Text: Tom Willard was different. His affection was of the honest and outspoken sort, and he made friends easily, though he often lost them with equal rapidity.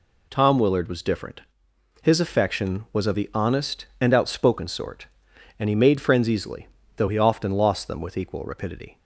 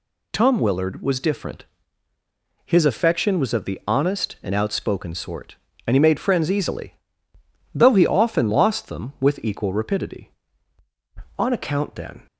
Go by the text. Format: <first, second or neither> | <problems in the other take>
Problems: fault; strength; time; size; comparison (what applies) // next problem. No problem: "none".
first | goes on to say "On account then"; noticeable; from 11.3 s on; 0.88 s long